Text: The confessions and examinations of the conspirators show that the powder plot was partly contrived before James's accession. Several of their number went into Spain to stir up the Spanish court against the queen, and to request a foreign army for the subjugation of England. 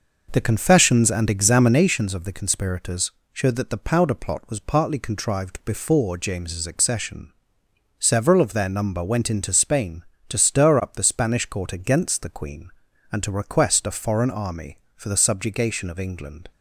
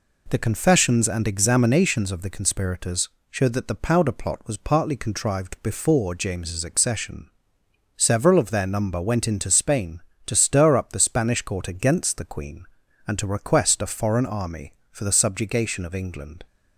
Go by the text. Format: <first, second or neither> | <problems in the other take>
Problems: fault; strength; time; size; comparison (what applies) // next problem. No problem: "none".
second | starts louder than the rest; noticeable; until 2.0 s; 5.5 dB // pauses between "conspirators" and "show"; slight; at 3.0 s; 0.24 s long; slight in the second